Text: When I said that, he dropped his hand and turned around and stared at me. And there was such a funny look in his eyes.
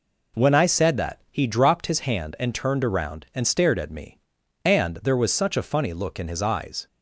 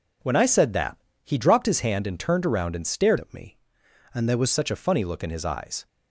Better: first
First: none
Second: changes voice from "at" to "was"; from 3.1 to 4.5 s; 1.4 s long

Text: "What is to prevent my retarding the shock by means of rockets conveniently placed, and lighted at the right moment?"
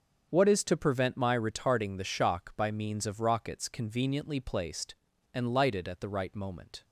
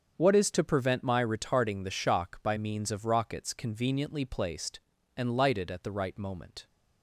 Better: neither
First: starts louder than the rest; until 1.3 s; 6.5 dB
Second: starts louder than the rest; until 1.1 s; 7 dB

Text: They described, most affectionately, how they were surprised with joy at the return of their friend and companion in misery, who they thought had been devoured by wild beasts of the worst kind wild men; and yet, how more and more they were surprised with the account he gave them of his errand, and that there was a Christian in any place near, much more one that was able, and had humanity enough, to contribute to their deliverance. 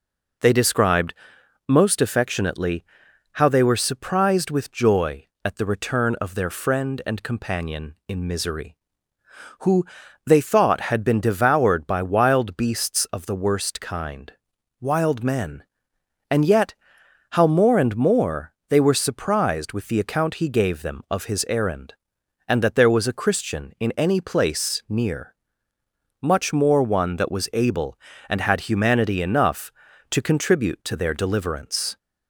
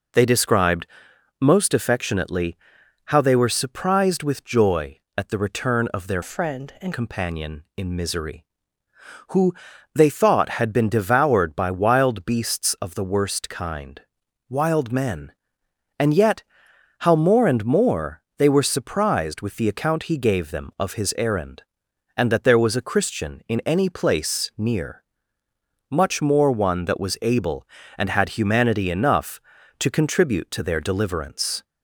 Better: first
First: pauses between "who" and "they"; at 9.8 s; 0.42 s long // pauses between "kind" and "wild"; noticeable; at 14.3 s; 0.50 s long // pauses between "more" and "they"; slight; at 18.5 s; 0.18 s long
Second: changes voice from "friend" to "and"; from 6.2 to 6.9 s; 0.7 s long // pauses between "who" and "they"; at 9.5 s; 0.42 s long // pauses between "kind" and "wild"; noticeable; at 14.0 s; 0.50 s long // pauses between "more" and "they"; slight; at 18.2 s; 0.18 s long

